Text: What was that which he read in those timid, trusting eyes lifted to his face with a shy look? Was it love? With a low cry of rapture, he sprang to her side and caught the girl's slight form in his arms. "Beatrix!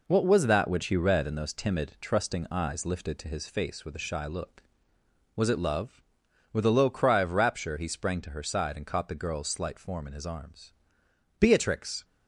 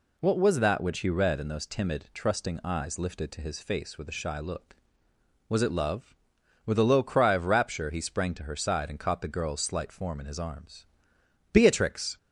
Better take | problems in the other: second | gets quieter; noticeable; throughout; 5.5 dB

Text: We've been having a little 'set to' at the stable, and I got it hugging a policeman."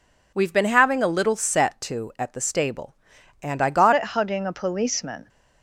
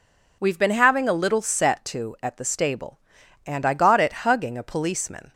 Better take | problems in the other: second | changes voice at "it"; from 3.9 s on; 1.3 s long

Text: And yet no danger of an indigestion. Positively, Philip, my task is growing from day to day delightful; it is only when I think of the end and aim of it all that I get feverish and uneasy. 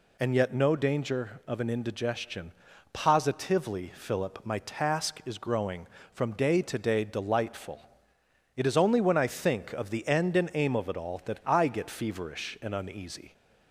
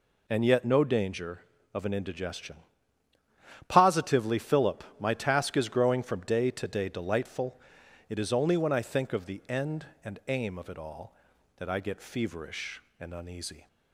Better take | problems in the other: neither | none

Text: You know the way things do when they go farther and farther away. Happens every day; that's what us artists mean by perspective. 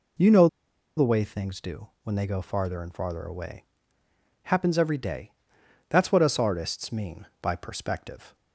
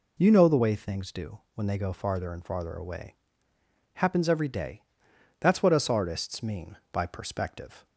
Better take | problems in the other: second | pauses between "know" and "the"; noticeable; at 0.4 s; 0.49 s long // pauses between "do" and "when"; slight; at 1.8 s; 0.16 s long; slight in the second

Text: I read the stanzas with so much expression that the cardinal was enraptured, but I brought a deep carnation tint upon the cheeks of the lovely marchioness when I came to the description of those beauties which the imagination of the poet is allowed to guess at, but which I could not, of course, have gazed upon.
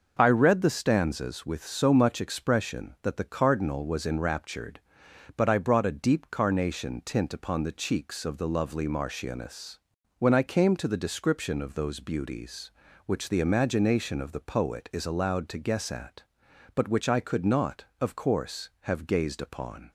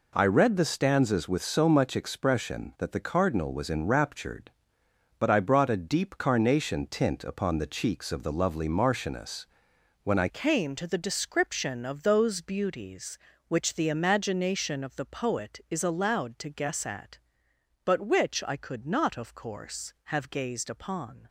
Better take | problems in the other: first | pauses between "marchioness" and "when"; noticeable; at 9.4 s; 0.56 s long; also in the first // changes voice at "came"; from 10.2 s on; 11.0 s long

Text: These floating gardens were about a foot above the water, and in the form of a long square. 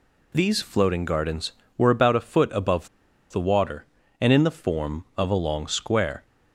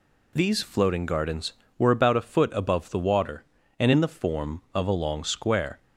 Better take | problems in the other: second | pauses between "above" and "the"; at 2.8 s; 0.43 s long

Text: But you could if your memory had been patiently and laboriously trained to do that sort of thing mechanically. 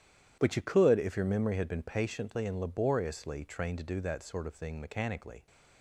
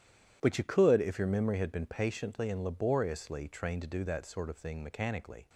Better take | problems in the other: neither | starts louder than the rest; strong; the same in both

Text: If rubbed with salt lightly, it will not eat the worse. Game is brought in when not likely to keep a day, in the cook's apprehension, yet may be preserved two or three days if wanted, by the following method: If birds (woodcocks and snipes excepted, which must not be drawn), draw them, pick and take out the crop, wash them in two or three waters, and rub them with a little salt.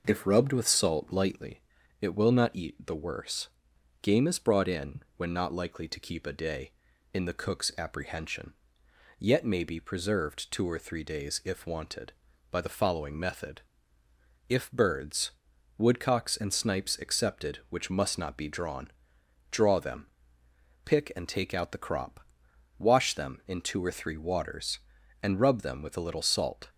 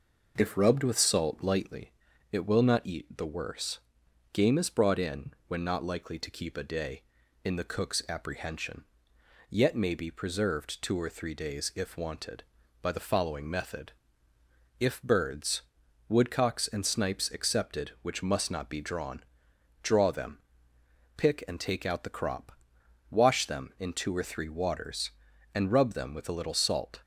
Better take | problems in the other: neither | pauses between "in" and "when"; slight; the same in both

